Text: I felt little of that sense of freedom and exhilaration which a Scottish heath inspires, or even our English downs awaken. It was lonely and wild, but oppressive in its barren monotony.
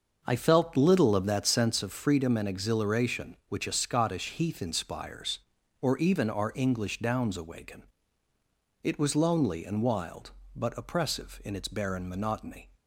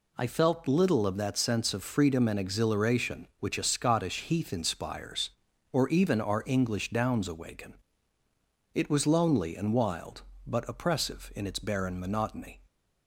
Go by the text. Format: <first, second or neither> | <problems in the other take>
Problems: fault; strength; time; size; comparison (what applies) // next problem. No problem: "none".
second | starts louder than the rest; until 1.8 s; 6.5 dB